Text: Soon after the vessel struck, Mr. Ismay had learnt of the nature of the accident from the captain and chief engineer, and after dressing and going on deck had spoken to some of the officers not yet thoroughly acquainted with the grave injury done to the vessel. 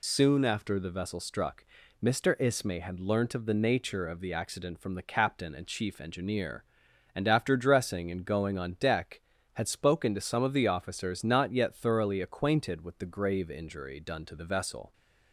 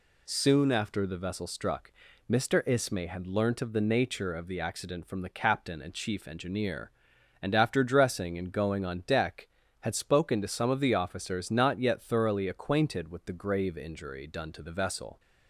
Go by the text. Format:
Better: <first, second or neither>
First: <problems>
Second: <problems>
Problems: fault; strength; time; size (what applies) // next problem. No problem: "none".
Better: second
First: loses the start of "Soon"; at 0.0 s; 25 ms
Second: none